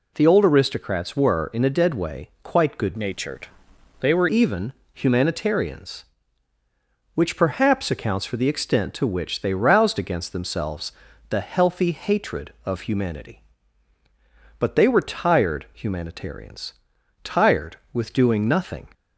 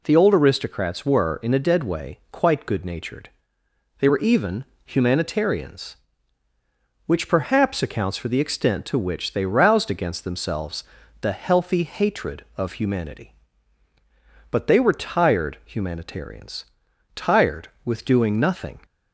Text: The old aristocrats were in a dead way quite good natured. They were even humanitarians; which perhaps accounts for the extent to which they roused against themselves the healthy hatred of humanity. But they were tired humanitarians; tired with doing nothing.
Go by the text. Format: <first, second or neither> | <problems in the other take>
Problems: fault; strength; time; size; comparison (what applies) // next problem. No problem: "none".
second | changes voice from "natured" to "were"; from 2.9 to 4.2 s; 1.3 s long // pauses between "even" and "humanitarians"; slight; at 4.7 s; 0.22 s long; slight in the second // pauses between "themselves" and "the"; slight; at 10.9 s; 0.36 s long; slight in the second